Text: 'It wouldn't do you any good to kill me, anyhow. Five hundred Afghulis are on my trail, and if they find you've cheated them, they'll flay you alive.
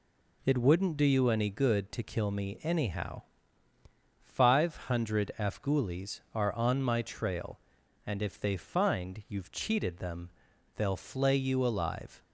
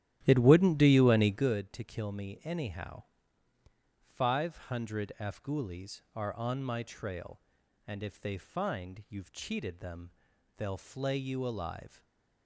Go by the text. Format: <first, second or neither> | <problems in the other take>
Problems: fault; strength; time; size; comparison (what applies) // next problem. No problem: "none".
first | starts louder than the rest; strong; until 1.6 s; 12.5 dB // stays silent after the last word; slight; from 11.8 s on; 0.6 s long